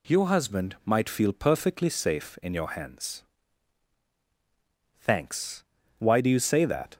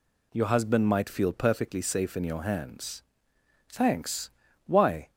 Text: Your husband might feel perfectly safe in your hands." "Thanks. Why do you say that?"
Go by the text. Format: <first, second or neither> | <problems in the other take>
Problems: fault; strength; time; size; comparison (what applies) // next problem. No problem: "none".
first | stops before "do you say that"; at 5.0 s